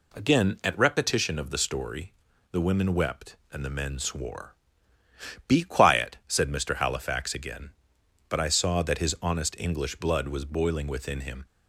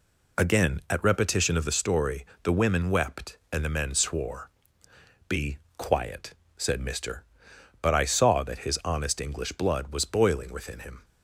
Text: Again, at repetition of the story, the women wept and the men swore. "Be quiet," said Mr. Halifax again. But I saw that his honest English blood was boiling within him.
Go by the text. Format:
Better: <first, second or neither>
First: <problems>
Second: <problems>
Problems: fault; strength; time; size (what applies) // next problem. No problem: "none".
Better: first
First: none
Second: pauses between "Be" and "quiet"; slight; at 5.5 s; 0.18 s long // skips "Halifax again"; at 7.5 s